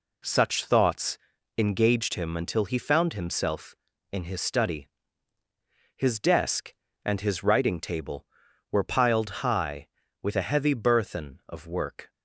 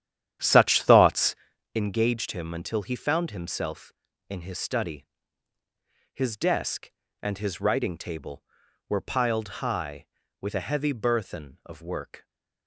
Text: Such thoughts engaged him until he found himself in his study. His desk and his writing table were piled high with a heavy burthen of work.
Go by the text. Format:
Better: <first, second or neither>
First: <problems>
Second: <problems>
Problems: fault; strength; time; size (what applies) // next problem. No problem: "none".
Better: first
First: pauses between "thoughts" and "engaged"; at 1.1 s; 0.40 s long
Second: starts louder than the rest; strong; until 1.7 s; 10.5 dB // pauses between "thoughts" and "engaged"; at 1.3 s; 0.40 s long